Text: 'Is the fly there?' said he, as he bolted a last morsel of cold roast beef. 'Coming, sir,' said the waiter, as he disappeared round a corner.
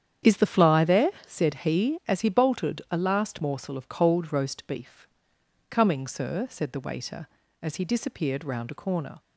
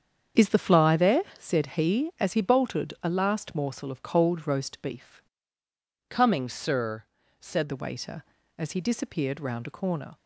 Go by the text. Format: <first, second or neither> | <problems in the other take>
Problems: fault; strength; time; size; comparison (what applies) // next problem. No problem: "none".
first | starts louder than the rest; strong; until 1.5 s; 7.5 dB; strong in the first // changes voice from "Coming" to "said"; from 6.0 to 7.6 s; 1.6 s long